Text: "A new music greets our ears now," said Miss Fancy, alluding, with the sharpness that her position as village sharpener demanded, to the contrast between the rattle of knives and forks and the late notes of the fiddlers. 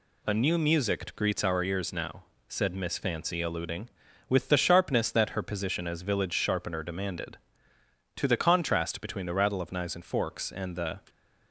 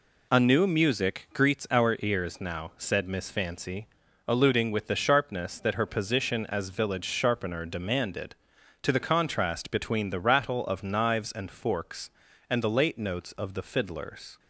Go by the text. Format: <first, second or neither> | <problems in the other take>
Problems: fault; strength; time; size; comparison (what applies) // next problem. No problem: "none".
second | stops before "late notes of the fiddlers"; at 11.0 s